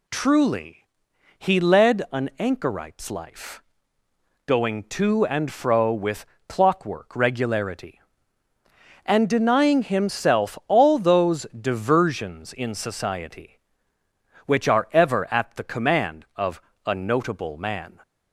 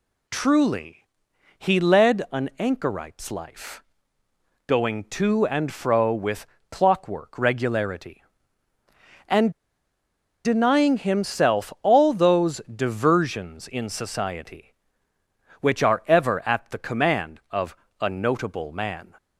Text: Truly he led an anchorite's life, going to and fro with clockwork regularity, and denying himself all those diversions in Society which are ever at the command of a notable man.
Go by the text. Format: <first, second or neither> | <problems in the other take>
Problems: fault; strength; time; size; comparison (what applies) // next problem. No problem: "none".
first | pauses between "Truly" and "he"; noticeable; at 1.0 s; 0.50 s long; noticeable in the first // pauses between "with" and "clockwork"; slight; at 6.4 s; 0.24 s long; slight in the first // pauses between "and" and "denying"; noticeable; at 9.5 s; 0.93 s long // pauses between "of" and "a"; slight; at 17.7 s; 0.24 s long; slight in the first